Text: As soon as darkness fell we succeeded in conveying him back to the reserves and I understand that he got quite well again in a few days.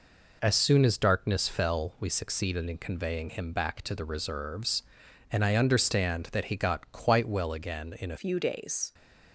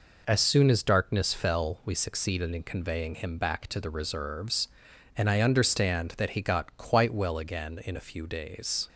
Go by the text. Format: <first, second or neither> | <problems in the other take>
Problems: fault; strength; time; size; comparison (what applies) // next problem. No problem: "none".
second | changes voice at "few"; from 8.1 s on; 0.8 s long